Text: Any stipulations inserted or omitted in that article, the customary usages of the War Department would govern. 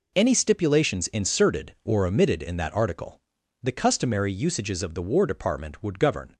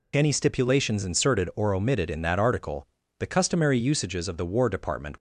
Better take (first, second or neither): first